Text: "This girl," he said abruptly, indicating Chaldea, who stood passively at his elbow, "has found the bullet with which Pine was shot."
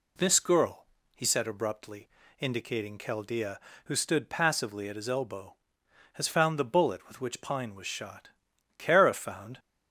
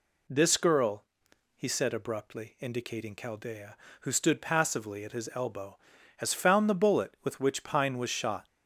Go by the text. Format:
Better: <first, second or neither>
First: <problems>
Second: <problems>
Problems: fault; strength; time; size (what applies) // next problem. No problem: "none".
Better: second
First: goes on to say "Kara found"; noticeable; from 8.7 s on; 0.80 s long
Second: none